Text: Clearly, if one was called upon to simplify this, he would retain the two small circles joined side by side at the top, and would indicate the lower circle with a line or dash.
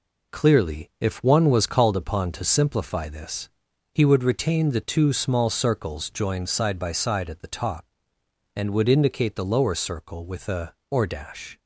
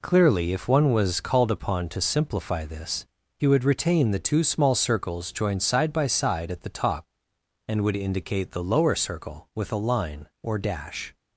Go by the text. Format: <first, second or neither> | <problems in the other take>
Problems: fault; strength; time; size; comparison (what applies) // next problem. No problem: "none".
second | skips "line"; at 10.8 s